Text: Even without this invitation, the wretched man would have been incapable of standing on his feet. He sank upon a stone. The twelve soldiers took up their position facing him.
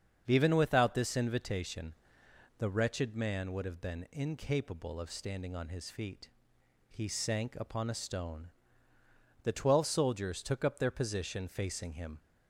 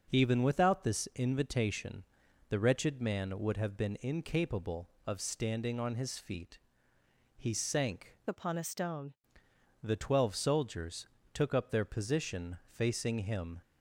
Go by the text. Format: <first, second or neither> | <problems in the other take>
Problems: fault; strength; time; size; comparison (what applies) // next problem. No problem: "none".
first | starts louder than the rest; noticeable; until 1.1 s; 6 dB; strong in the first // changes voice from "upon" to "stone"; from 8.2 to 9.1 s; 0.9 s long // pauses between "soldiers" and "took"; slight; at 11.0 s; 0.26 s long